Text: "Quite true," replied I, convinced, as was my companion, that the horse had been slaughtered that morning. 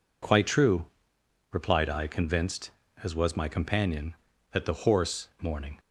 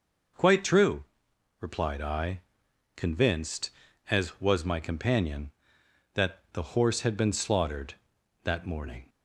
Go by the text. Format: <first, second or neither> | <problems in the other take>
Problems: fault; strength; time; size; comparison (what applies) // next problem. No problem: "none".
second | skips "had been slaughtered that"; at 5.3 s